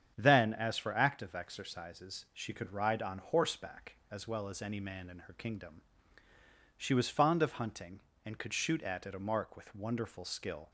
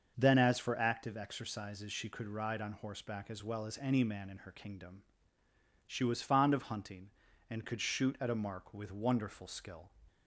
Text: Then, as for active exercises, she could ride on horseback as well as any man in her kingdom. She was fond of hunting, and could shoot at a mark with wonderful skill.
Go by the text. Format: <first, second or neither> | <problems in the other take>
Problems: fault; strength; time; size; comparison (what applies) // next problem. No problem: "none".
second | starts louder than the rest; strong; until 1.1 s; 8 dB; also in the second // says "at" twice; at 9.0 s